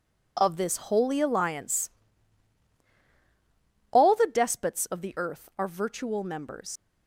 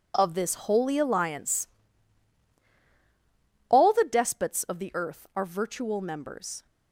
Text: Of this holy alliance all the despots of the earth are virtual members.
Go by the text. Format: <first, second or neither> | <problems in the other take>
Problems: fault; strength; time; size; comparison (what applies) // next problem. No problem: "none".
second | pauses between "alliance" and "all"; strong; at 1.8 s; 2.0 s long; strong in the second // leaves "members" unfinished; at 6.7 s; 120 ms